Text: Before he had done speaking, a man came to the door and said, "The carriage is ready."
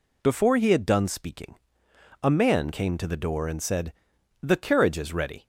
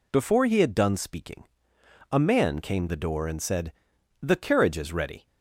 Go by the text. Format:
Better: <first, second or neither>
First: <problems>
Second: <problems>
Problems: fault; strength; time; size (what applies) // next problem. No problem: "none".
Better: first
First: none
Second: skips "to"; at 2.8 s